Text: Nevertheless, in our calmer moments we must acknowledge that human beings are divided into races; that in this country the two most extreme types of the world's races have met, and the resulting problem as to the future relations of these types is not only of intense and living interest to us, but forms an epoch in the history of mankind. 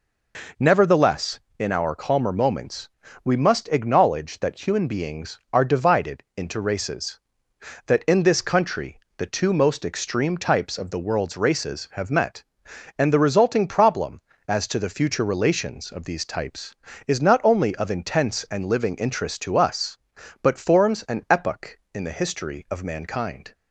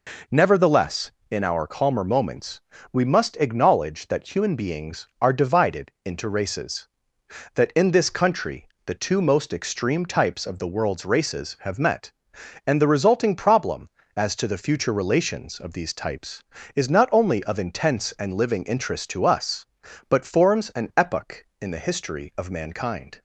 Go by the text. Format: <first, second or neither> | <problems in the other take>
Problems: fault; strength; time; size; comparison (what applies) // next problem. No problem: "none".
neither | pauses between "moments" and "we"; slight; the same in both // pauses between "country" and "the"; slight; the same in both